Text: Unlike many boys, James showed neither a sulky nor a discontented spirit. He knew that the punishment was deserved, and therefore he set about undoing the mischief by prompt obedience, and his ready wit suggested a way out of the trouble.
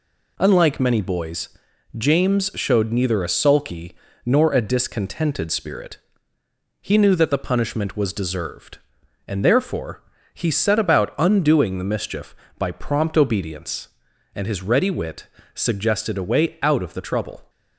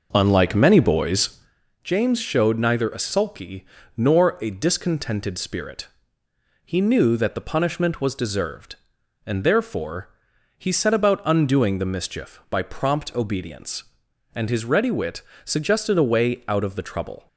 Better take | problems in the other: first | starts louder than the rest; noticeable; until 1.7 s; 5.5 dB // pauses between "sulky" and "nor"; slight; at 3.6 s; 0.30 s long; slight in the first // pauses between "therefore" and "he"; noticeable; at 10.0 s; 0.48 s long; slight in the first // pauses between "wit" and "suggested"; slight; at 15.2 s; 0.22 s long; slight in the first

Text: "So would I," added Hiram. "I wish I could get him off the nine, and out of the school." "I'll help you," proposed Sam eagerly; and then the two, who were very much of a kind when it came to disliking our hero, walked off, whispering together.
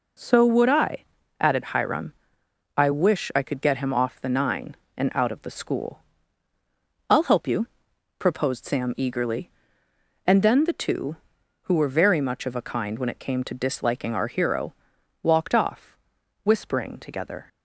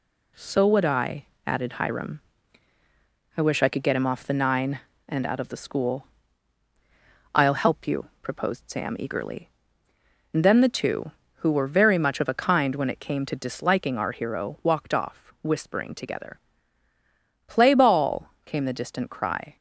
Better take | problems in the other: first | goes on to say "Play ball came the distant cry"; strong; from 17.4 s on; 2.1 s long

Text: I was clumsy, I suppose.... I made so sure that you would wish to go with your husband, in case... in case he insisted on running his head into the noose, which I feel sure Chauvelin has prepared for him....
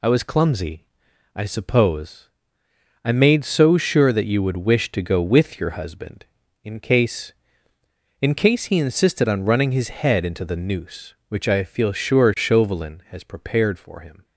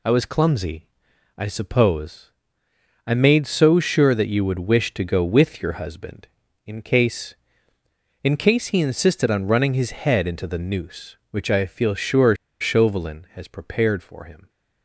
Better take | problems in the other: first | pauses between "sure" and "Chauvelin"; slight; at 12.3 s; 0.25 s long

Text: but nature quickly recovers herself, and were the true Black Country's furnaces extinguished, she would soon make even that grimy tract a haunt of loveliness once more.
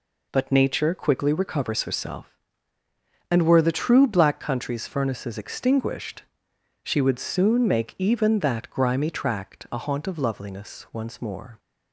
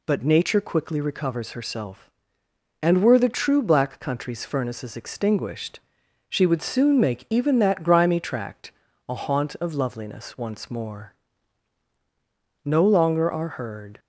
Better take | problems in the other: first | pauses between "tract" and "a"; slight; at 8.7 s; 0.36 s long // goes on to say "No longer are heard"; from 12.6 s on; 1.3 s long

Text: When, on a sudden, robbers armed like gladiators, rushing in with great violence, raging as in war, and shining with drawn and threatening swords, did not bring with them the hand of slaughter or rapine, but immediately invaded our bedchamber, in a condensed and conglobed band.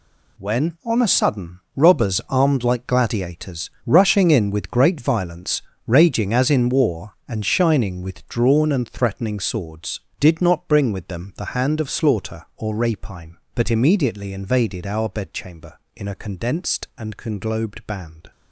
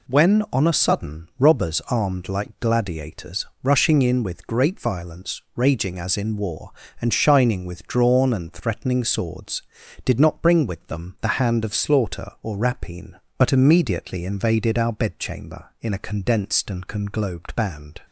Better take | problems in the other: second | gets quieter; strong; throughout; 11 dB

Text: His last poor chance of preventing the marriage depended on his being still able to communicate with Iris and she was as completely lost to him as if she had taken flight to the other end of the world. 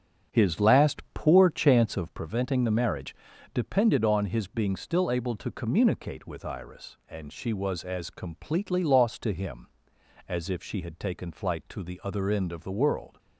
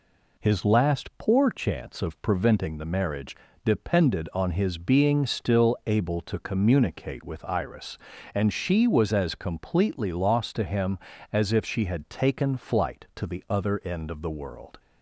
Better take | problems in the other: second | starts louder than the rest; strong; until 2.1 s; 8.5 dB // pauses between "marriage" and "depended"; slight; at 3.1 s; 0.36 s long; slight in the second

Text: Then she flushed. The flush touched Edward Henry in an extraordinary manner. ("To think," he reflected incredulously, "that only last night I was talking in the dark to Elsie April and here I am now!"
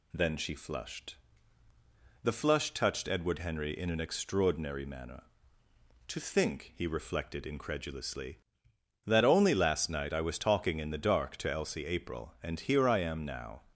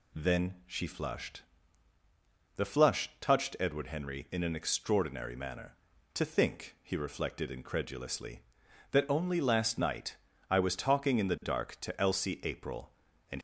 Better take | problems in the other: first | pauses between "night" and "I"; slight; at 10.1 s; 0.36 s long // stops before "here I am now"; at 13.3 s

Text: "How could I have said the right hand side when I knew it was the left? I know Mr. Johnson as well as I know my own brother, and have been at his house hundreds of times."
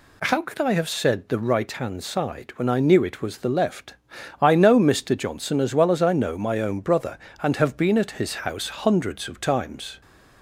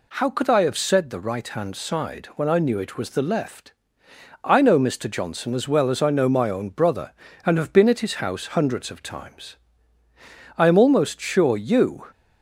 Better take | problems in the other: first | goes on to say "I am almost sure you"; from 10.5 s on; 1.5 s long

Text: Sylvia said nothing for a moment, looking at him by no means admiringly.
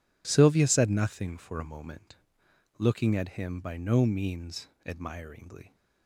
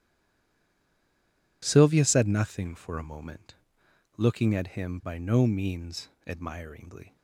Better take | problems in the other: first | stays silent before the first word; noticeable; until 1.6 s; 1.6 s long // pauses between "means" and "admiringly"; slight; at 6.0 s; 0.18 s long; slight in the first

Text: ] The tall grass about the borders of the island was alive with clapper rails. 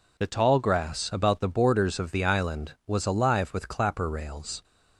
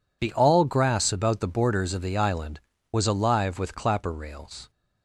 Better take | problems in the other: first | says "all" for "tall"; at 0.3 s

